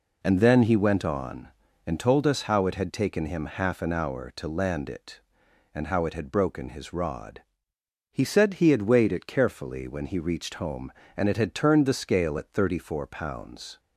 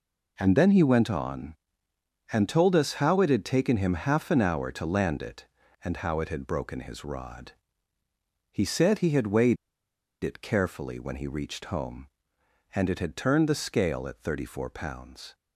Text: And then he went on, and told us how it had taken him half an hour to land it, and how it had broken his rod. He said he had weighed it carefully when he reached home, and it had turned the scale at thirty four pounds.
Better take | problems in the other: first | pauses between "weighed" and "it"; noticeable; at 9.5 s; 0.68 s long

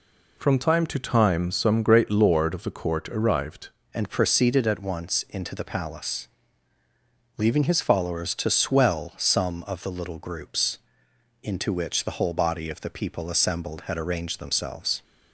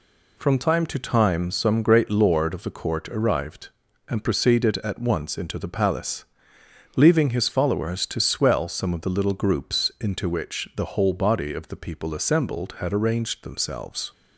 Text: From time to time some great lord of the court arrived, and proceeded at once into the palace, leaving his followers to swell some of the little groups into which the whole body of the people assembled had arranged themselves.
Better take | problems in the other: second | changes voice at "and"; from 3.9 s on; 11.1 s long // pauses between "groups" and "into"; noticeable; at 10.7 s; 0.64 s long

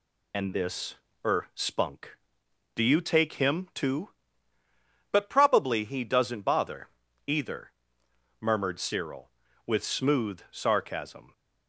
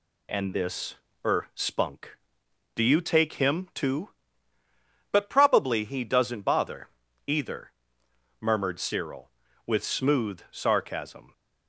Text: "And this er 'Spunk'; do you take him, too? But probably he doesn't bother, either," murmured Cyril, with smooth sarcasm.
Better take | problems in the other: second | loses the start of "And"; at 0.3 s; 55 ms // pauses between "this" and "er"; slight; at 0.9 s; 0.32 s long; slight in the second

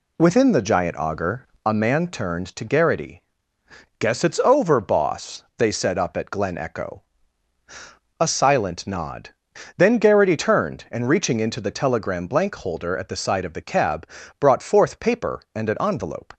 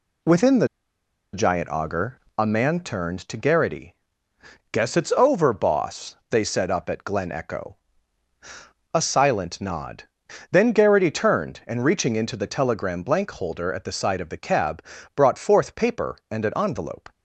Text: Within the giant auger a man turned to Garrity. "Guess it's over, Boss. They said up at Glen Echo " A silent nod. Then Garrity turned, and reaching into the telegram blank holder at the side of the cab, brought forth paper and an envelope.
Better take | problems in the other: first | pauses between "the" and "giant"; noticeable; at 0.6 s; 0.66 s long // pauses between "auger" and "a"; slight; at 2.1 s; 0.20 s long; slight in the first

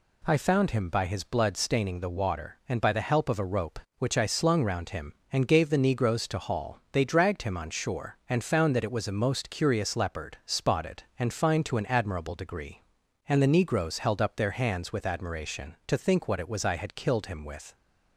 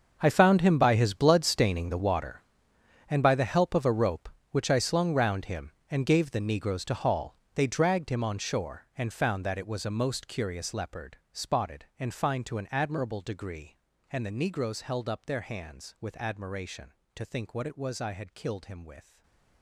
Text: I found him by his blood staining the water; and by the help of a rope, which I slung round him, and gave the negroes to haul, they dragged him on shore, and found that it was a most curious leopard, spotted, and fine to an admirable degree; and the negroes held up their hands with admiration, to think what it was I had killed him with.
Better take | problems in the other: first | gets quieter; strong; throughout; 16 dB // stays silent after the last word; slight; from 19.0 s on; 0.6 s long

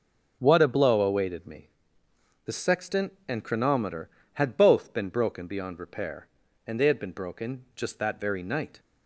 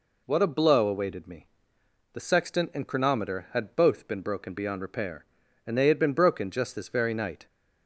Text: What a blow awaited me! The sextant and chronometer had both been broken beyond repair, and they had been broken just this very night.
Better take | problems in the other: second | says "that" for "this"; at 7.9 s

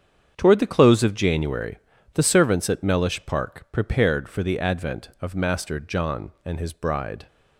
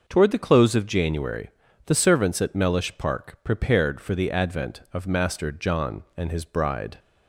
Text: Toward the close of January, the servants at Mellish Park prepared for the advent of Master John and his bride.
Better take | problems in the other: second | gets quieter; strong; throughout; 11.5 dB

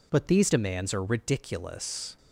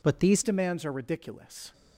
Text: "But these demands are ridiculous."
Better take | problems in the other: first | changes voice at "demands"; from 0.4 s on; 1.3 s long

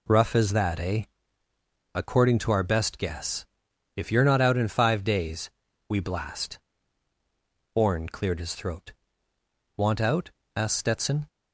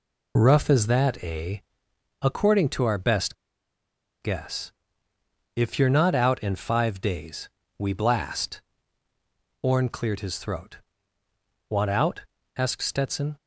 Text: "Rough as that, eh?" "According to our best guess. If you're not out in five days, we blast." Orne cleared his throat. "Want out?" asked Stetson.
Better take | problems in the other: first | pauses between "best" and "guess"; noticeable; at 3.3 s; 0.87 s long

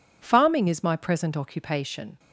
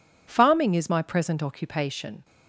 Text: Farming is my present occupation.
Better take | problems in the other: neither | none

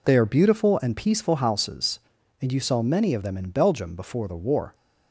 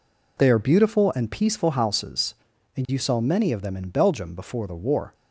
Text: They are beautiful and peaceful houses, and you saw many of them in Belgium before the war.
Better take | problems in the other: neither | none

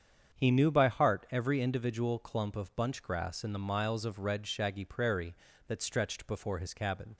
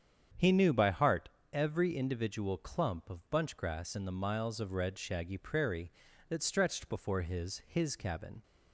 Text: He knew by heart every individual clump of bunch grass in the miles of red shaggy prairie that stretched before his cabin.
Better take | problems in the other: first | starts louder than the rest; strong; until 1.6 s; 8 dB; strong in the first // pauses between "heart" and "every"; slight; at 1.2 s; 0.24 s long // says "his" twice; at 7.6 s

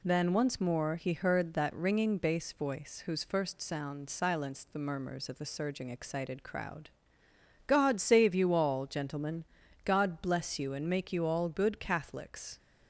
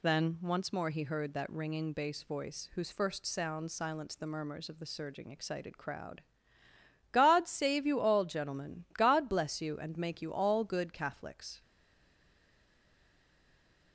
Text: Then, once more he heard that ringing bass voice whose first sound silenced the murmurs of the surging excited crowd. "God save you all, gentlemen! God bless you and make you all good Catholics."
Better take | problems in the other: first | stays silent after the last word; from 11.6 s on; 2.3 s long

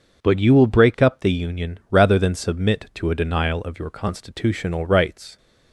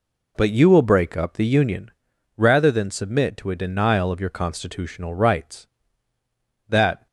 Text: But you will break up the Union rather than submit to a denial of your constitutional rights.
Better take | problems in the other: first | pauses between "Union" and "rather"; noticeable; at 1.9 s; 0.46 s long // goes on to say "That"; slight; from 6.6 s on; 0.38 s long

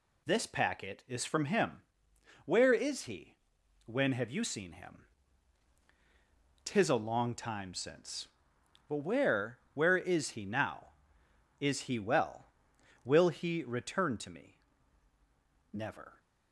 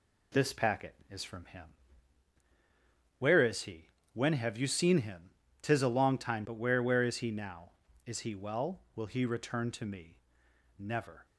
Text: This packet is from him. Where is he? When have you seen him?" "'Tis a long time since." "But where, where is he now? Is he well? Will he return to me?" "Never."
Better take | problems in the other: first | skips "since"; at 6.4 s

